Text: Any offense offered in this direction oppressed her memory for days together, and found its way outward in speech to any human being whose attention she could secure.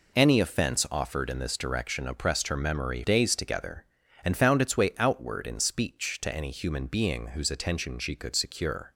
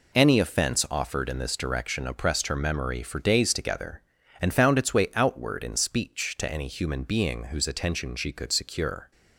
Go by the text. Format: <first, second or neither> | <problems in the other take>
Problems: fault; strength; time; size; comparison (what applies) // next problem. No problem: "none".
second | skips "for"; at 3.0 s